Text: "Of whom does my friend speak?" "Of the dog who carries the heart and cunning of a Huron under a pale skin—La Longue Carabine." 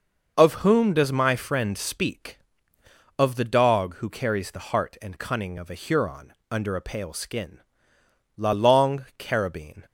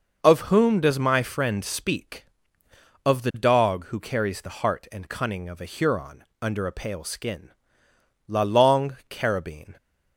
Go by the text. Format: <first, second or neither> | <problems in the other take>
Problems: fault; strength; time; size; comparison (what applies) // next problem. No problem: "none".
neither | pauses between "Huron" and "under"; slight; the same in both